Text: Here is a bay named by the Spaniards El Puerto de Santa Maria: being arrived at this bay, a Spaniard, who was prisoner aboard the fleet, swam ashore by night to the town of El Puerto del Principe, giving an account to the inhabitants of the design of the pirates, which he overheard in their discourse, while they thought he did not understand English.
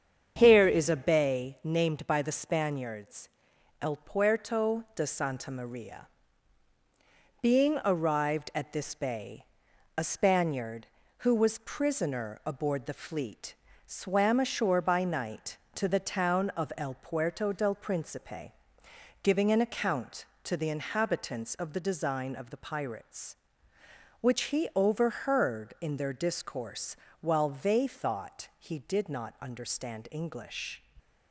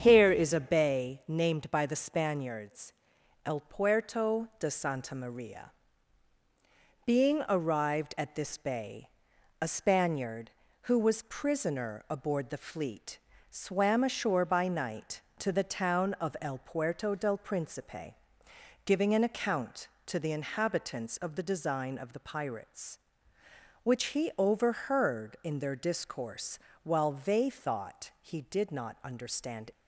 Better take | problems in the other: first | starts louder than the rest; strong; until 1.0 s; 8 dB; strong in the first // pauses between "Spaniards" and "El"; noticeable; at 2.9 s; 0.54 s long; noticeable in the first // stops before "English"; at 29.7 s

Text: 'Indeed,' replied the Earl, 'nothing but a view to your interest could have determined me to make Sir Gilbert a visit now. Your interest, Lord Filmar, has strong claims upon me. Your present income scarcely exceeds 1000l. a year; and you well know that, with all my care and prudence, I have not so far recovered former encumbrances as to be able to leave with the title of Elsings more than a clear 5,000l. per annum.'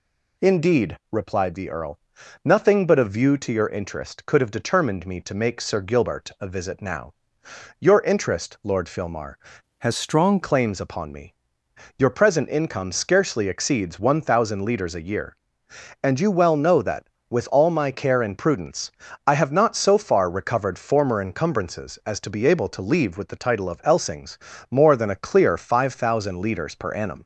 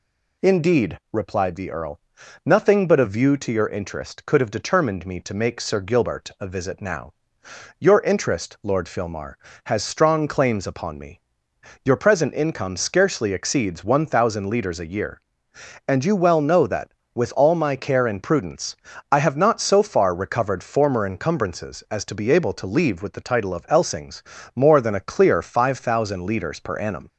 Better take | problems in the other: second | changes voice from "has" to "strong"; from 9.7 to 10.3 s; 0.6 s long // pauses between "Elsings" and "more"; slight; at 24.3 s; 0.32 s long; slight in the second

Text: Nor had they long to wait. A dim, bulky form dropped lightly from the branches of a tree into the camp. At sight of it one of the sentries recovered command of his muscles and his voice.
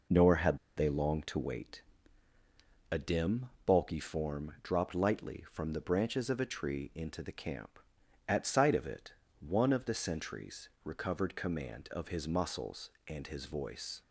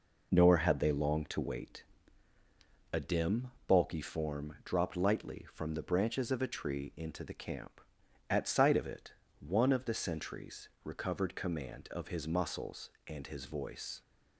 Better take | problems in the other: second | pauses between "had" and "they"; slight; at 0.5 s; 0.19 s long // pauses between "it" and "one"; slight; at 9.1 s; 0.26 s long; slight in the second // pauses between "sentries" and "recovered"; slight; at 10.6 s; 0.16 s long; slight in the second

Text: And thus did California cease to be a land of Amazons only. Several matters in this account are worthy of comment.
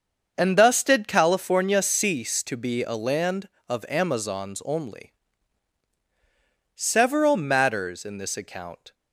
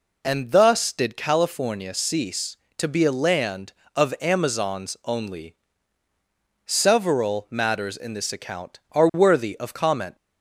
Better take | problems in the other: second | starts louder than the rest; until 1.3 s; 6.5 dB // stops before "are worthy of comment"; at 8.9 s

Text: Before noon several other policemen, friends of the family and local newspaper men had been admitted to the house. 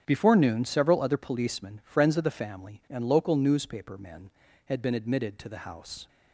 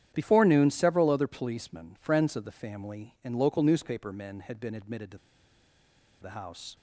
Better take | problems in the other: first | starts louder than the rest; strong; until 1.1 s; 10 dB; strong in the first // pauses between "to" and "the"; at 5.1 s; 1.0 s long

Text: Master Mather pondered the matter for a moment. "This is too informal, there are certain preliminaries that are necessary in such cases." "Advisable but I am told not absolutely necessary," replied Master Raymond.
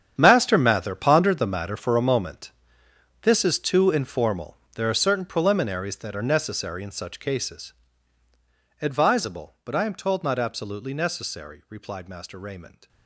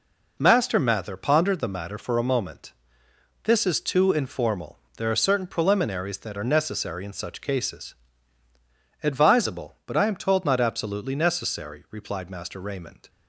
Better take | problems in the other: second | gets quieter; strong; throughout; 15 dB

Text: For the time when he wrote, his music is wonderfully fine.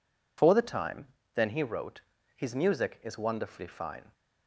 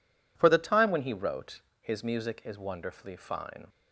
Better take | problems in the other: second | says "then" for "when"; at 1.3 s

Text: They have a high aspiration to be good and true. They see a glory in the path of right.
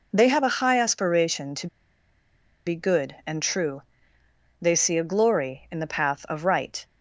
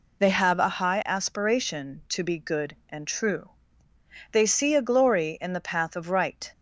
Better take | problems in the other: second | pauses between "to" and "be"; at 1.6 s; 0.98 s long

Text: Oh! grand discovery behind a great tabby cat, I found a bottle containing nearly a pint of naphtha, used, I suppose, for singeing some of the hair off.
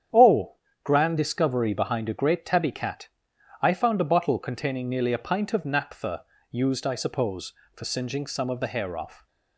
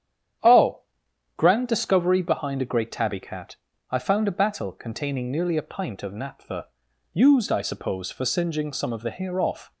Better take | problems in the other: first | starts louder than the rest; strong; until 1.9 s; 9.5 dB; strong in the first // says "battle" for "bottle"; at 4.3 s

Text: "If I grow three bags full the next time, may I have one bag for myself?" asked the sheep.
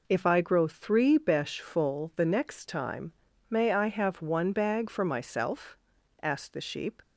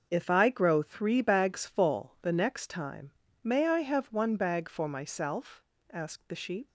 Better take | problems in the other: second | says "besh" for "bags"; at 1.1 s

